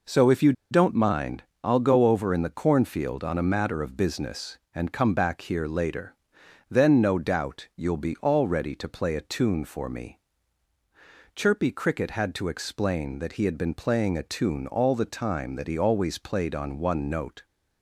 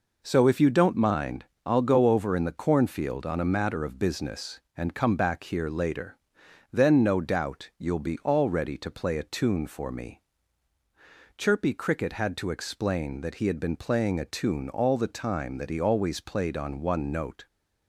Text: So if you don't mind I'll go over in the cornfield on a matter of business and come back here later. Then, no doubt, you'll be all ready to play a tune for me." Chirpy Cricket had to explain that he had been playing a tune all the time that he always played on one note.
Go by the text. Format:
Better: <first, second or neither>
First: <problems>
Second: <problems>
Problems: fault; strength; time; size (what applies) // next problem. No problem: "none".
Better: second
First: pauses between "you" and "don't"; slight; at 0.5 s; 0.18 s long // pauses between "mind" and "I'll"; slight; at 1.4 s; 0.20 s long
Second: pauses between "mind" and "I'll"; slight; at 1.4 s; 0.20 s long